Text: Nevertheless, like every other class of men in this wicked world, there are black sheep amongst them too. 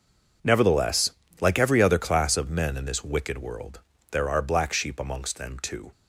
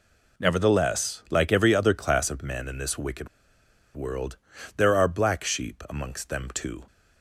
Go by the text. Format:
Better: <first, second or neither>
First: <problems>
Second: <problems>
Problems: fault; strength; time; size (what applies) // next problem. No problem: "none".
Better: first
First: none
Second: pauses between "wicked" and "world"; noticeable; at 3.2 s; 0.68 s long